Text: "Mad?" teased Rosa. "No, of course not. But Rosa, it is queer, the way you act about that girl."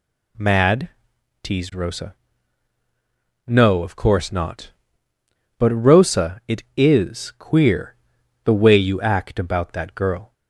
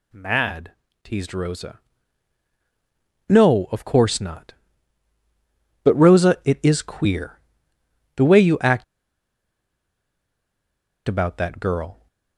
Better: first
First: none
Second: pauses between "act" and "about"; strong; at 8.8 s; 2.2 s long

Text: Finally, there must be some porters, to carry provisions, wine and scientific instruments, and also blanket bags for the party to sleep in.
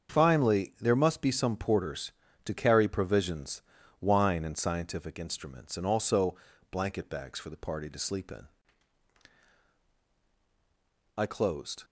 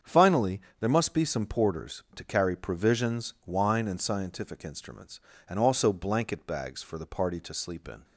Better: second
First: starts louder than the rest; until 1.1 s; 7 dB // pauses between "also" and "blanket"; at 6.3 s; 0.38 s long // goes on to say "I closed"; noticeable; from 11.1 s on; 0.68 s long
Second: starts louder than the rest; strong; until 1.2 s; 7.5 dB

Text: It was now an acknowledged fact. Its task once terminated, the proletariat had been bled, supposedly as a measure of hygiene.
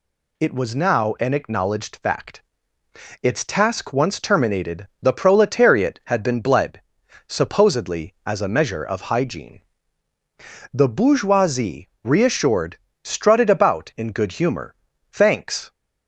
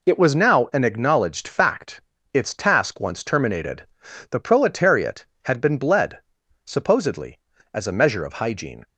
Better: second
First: goes on to say "The bourgeoisie reassured strutted about in good humor thanks"; strong; from 10.7 s on; 4.9 s long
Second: none

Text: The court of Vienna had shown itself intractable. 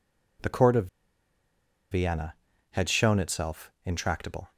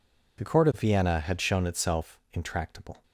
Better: second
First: pauses between "of" and "Vienna"; at 0.8 s; 1.0 s long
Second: none

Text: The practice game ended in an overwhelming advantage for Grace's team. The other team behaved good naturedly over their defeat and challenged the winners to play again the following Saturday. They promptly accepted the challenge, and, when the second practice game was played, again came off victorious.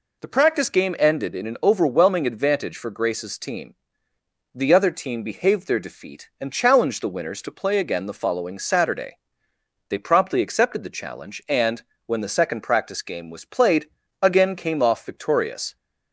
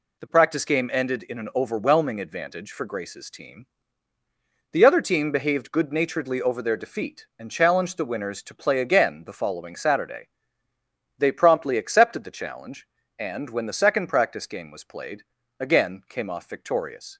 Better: second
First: skips "good naturedly over"; at 5.6 s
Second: none

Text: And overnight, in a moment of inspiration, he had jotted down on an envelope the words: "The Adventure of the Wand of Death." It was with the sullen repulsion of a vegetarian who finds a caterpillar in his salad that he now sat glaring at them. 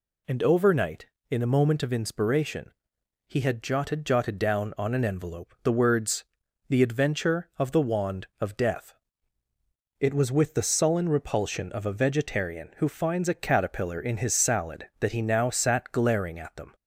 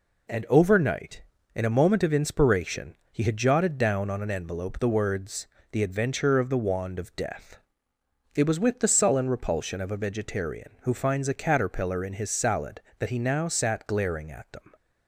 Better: second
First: says "jotted" twice; at 4.0 s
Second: none

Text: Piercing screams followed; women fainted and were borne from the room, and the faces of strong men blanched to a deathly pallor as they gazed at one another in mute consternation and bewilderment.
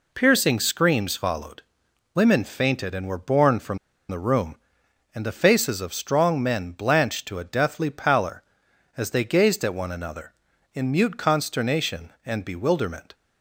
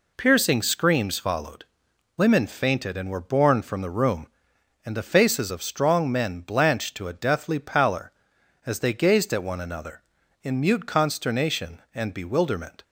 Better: second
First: pauses between "from" and "the"; slight; at 3.7 s; 0.32 s long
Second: none

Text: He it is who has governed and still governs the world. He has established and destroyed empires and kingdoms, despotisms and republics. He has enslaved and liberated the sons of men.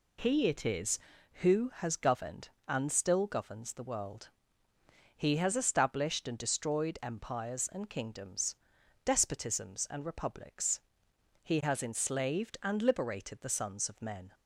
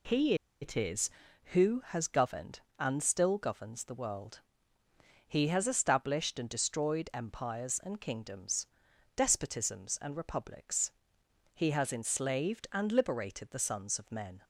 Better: first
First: none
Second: pauses between "He" and "it"; slight; at 0.3 s; 0.27 s long

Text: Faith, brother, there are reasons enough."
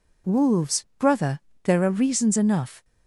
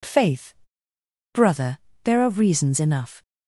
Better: second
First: says "Wolves" for "Faith"; at 0.2 s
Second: none

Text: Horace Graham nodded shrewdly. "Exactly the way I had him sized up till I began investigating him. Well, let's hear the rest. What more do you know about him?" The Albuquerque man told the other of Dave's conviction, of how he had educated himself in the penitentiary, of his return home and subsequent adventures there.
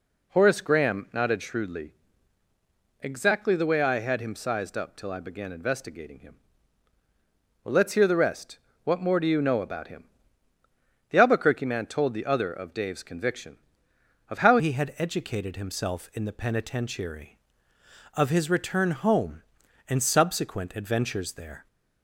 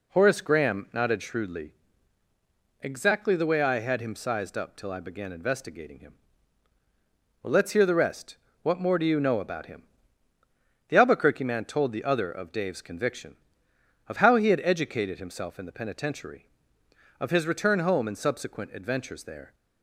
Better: second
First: changes voice at "he"; from 14.5 s on; 7.1 s long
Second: none

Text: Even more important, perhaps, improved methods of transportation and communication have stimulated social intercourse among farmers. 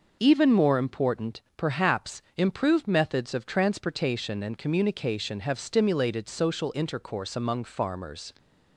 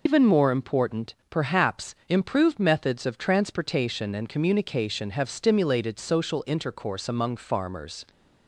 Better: first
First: none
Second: loses the start of "Even"; at 0.0 s; 120 ms

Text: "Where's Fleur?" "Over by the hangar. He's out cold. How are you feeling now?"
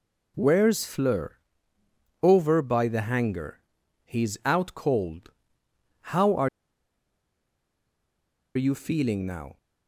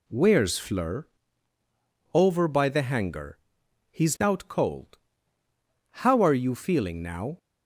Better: second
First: pauses between "are" and "you"; strong; at 6.4 s; 2.0 s long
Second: none

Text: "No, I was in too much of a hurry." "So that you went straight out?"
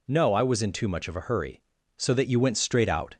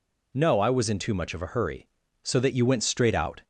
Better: neither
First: none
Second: none

